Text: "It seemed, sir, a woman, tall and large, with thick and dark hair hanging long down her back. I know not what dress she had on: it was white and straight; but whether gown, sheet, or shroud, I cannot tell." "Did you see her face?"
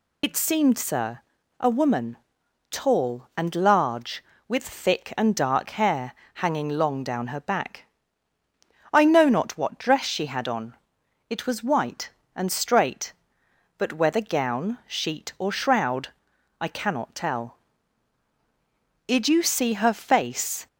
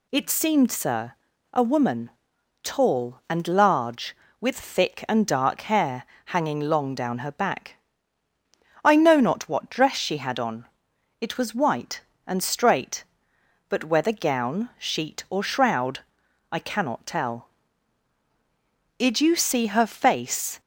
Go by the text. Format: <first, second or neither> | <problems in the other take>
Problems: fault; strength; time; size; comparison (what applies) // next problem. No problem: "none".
second | loses the start of "It"; at 0.2 s; 65 ms // pauses between "hair" and "hanging"; slight; at 6.1 s; 0.22 s long; slight in the second